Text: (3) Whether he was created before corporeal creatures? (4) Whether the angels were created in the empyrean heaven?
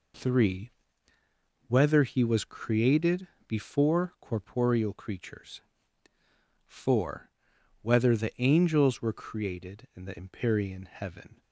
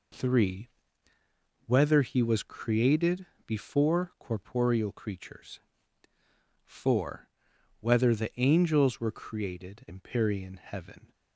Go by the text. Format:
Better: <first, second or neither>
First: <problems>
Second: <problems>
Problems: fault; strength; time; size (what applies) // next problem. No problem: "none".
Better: first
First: pauses between "created" and "before"; slight; at 3.2 s; 0.22 s long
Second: pauses between "created" and "before"; slight; at 3.2 s; 0.22 s long // skips "in the"; at 9.8 s